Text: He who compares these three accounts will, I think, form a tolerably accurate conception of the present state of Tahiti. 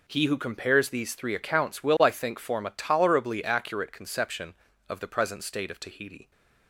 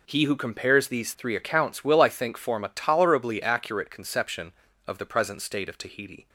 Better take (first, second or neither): neither